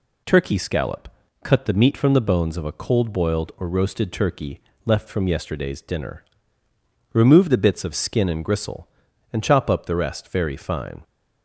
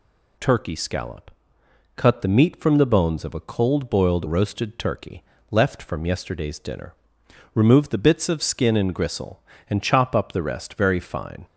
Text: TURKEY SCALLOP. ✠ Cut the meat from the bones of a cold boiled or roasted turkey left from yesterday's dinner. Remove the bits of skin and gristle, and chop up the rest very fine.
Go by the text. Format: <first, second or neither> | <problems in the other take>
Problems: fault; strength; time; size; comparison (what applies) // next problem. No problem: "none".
first | skips "or"; at 4.2 s // pauses between "turkey" and "left"; slight; at 5.2 s; 0.28 s long; slight in the first